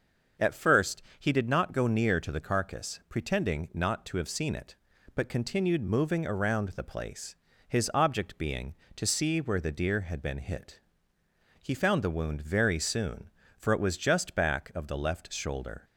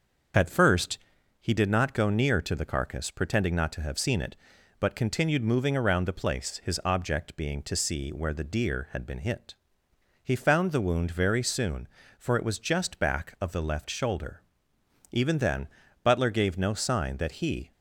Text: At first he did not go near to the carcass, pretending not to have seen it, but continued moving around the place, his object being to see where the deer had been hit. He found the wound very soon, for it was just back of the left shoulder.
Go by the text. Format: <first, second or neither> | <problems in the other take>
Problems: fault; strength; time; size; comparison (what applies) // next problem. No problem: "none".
first | starts louder than the rest; until 1.7 s; 6.5 dB; also in the first // pauses between "first" and "he"; at 0.9 s; 0.42 s long; slight in the first // goes on to say "Even then Butler gave no sign that he"; strong; from 15.1 s on; 2.6 s long